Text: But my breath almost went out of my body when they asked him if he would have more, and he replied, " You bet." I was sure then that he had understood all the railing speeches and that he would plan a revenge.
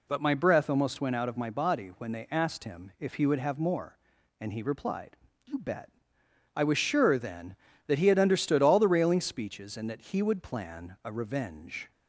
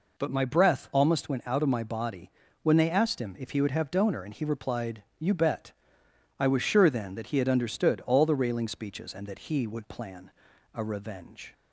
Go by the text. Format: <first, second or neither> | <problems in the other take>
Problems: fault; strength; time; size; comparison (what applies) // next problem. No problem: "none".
first | pauses between "body" and "when"; slight; at 2.3 s; 0.32 s long // says "donor" for "more"; at 3.9 s // pauses between "plan" and "a"; at 10.3 s; 0.42 s long